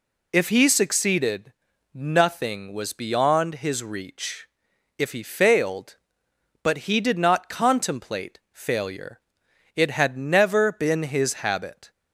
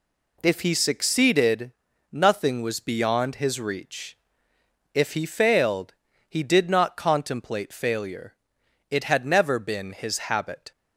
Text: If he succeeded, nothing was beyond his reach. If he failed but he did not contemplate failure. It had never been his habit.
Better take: first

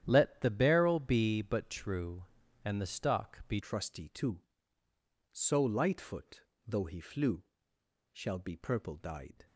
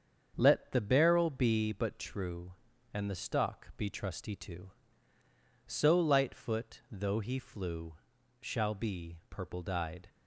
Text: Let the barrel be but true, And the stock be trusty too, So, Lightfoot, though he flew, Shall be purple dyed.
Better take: second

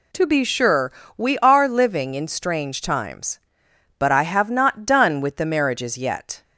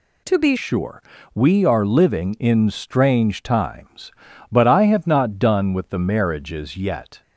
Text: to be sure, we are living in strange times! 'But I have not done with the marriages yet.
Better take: first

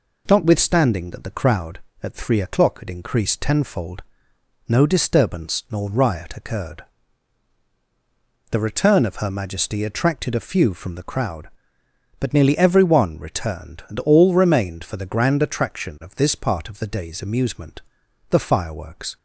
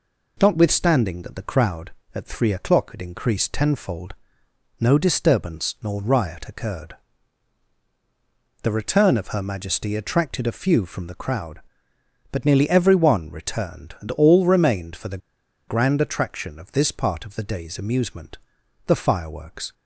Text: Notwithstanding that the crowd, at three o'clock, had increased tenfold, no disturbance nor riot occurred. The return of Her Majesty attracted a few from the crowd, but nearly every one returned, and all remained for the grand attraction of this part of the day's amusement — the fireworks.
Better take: first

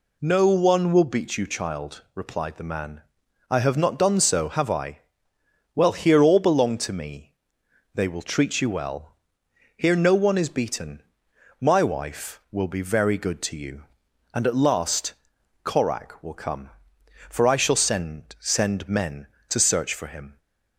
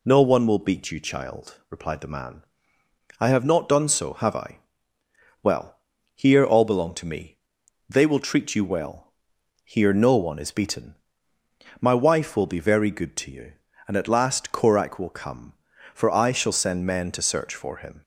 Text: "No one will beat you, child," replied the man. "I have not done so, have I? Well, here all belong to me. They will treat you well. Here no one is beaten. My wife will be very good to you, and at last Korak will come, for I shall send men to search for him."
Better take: second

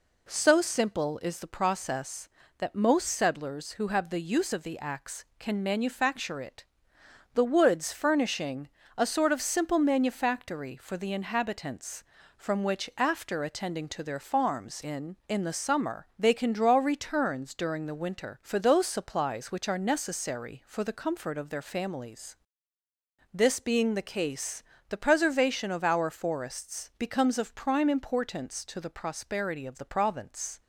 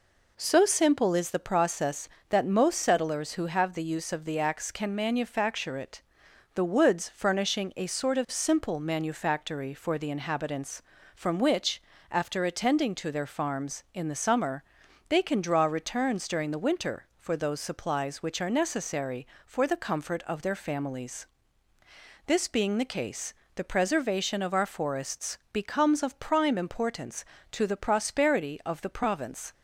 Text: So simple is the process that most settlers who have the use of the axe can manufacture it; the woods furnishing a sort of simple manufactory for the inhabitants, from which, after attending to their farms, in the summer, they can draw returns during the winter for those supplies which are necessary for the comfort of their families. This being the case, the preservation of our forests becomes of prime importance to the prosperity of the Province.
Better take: second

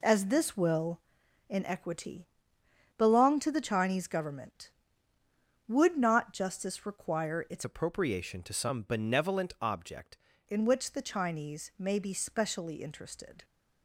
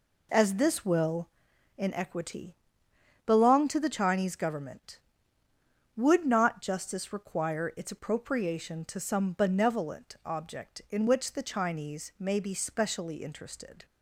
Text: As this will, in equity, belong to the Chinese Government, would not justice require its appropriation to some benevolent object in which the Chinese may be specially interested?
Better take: second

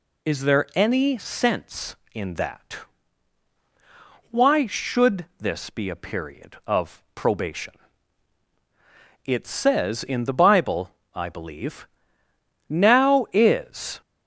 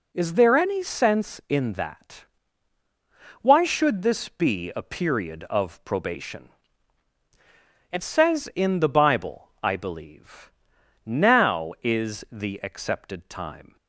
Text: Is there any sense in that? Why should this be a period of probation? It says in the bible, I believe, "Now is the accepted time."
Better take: second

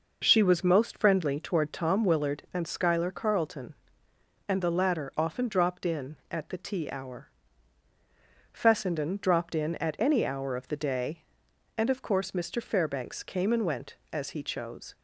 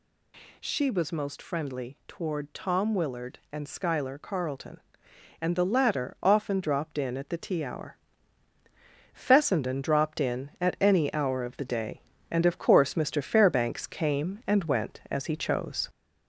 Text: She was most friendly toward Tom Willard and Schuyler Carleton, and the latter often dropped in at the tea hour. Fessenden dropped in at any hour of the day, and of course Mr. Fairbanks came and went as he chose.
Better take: first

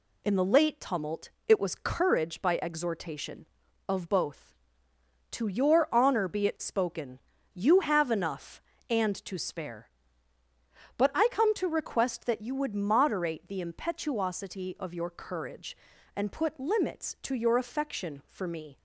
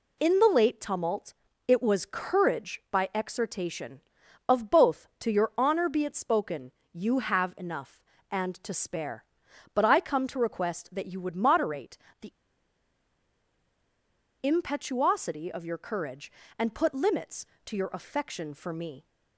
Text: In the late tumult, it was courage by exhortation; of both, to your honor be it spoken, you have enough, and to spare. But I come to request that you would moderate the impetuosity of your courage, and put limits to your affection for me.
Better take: first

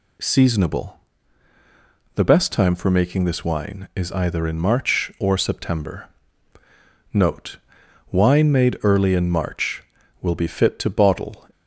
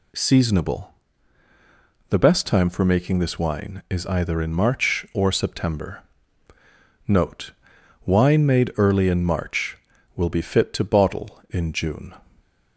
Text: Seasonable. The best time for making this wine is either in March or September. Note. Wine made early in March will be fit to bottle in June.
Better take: second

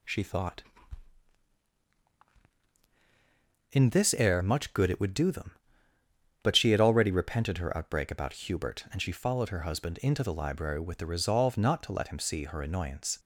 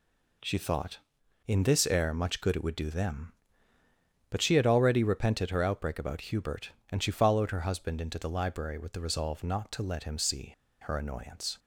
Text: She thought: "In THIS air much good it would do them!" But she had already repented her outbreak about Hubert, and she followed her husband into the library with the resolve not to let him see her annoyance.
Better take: first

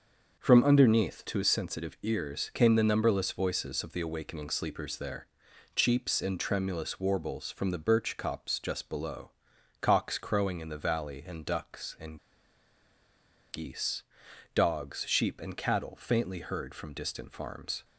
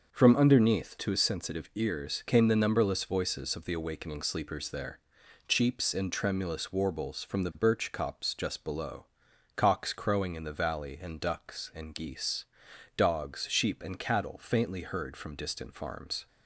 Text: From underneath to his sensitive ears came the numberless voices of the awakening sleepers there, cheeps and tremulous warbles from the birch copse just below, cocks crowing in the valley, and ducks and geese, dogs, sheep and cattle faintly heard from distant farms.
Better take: second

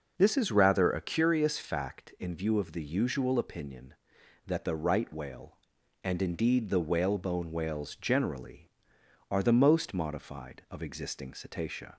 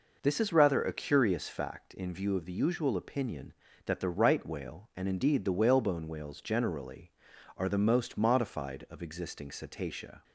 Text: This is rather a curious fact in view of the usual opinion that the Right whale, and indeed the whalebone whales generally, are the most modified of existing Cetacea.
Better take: neither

